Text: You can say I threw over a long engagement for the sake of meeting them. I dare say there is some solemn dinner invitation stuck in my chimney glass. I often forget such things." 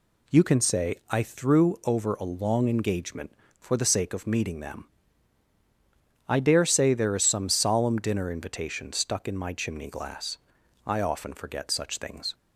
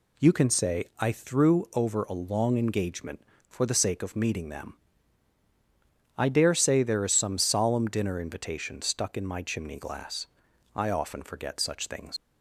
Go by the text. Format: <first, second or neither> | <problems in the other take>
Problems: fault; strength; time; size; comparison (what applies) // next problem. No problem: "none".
first | leaves "things" unfinished; at 12.1 s; 65 ms